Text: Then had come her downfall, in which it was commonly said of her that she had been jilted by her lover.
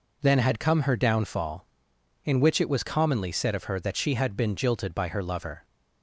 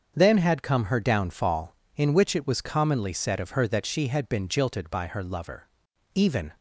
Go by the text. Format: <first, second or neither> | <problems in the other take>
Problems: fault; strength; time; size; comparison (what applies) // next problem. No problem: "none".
first | starts louder than the rest; until 1.1 s; 7 dB // goes on to say "Even"; slight; from 6.1 s on; 0.40 s long